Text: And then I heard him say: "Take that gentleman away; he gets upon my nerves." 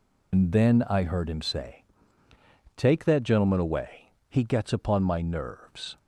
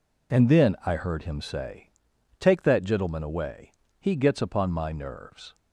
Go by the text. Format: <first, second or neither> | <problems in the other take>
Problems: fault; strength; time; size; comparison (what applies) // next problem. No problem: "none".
second | loses the start of "And"; at 0.3 s; 75 ms